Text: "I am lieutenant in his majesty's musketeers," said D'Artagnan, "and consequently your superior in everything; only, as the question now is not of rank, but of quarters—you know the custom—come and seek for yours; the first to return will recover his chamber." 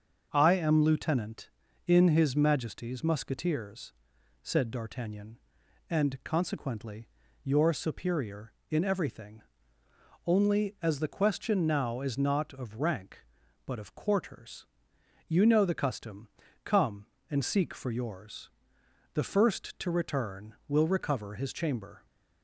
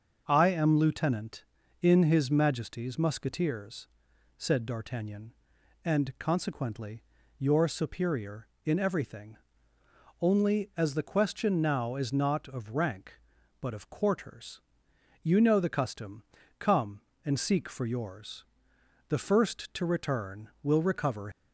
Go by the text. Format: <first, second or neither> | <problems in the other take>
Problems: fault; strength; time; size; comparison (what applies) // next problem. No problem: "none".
first | starts louder than the rest; until 1.2 s; 6.5 dB; also in the first // pauses between "consequently" and "your"; slight; at 7.0 s; 0.34 s long; slight in the first // stops before "his chamber"; at 21.3 s